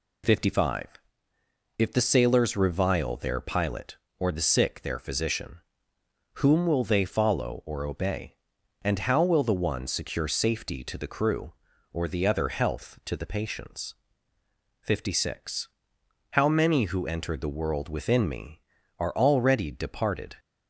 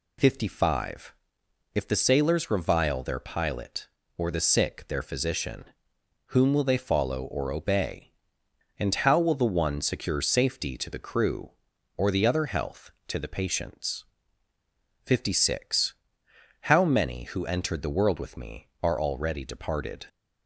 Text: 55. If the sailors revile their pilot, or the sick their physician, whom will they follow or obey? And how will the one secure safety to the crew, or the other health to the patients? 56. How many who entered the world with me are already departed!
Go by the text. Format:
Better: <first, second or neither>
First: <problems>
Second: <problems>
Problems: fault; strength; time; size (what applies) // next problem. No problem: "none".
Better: second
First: says "within" for "with"; at 17.8 s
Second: none